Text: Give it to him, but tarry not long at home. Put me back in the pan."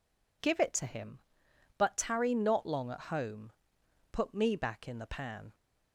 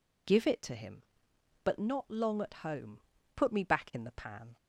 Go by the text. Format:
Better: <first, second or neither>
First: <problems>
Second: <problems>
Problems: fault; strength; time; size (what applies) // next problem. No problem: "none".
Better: first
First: none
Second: skips "tarry"; at 1.7 s